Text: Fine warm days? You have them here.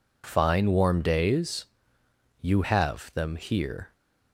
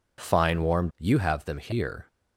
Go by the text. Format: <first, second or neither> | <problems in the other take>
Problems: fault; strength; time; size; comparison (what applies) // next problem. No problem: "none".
first | skips "days"; at 0.9 s